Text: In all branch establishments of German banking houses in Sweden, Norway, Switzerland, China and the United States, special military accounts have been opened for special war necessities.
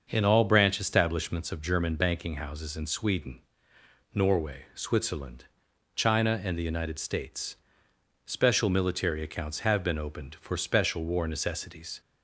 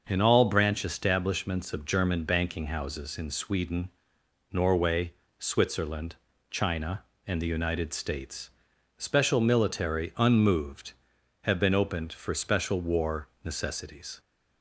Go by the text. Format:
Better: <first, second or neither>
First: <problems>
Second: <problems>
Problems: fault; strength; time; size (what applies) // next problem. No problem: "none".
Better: first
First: starts louder than the rest; until 1.1 s; 6.5 dB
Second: starts louder than the rest; until 1.0 s; 6 dB // says "unmoved" for "accounts"; at 10.1 s // pauses between "war" and "necessities"; slight; at 13.2 s; 0.18 s long